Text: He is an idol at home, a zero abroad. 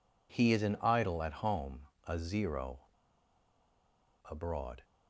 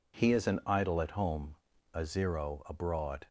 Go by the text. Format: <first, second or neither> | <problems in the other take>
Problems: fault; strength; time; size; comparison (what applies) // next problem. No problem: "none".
second | pauses between "zero" and "abroad"; strong; at 2.7 s; 1.4 s long